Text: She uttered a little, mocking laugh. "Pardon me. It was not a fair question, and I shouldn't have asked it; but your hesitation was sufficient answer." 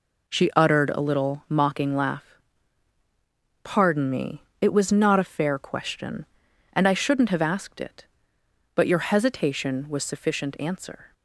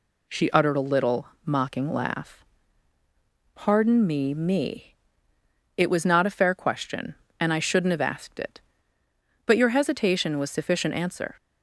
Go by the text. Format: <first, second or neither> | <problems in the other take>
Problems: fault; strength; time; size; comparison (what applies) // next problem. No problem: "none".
first | says "me" twice; at 4.3 s